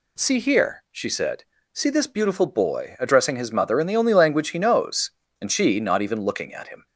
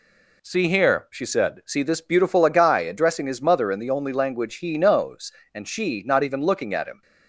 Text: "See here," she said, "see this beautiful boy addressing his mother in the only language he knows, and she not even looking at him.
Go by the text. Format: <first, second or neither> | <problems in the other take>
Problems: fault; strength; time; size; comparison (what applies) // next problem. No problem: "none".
first | says "agai" for "boy"; at 2.4 s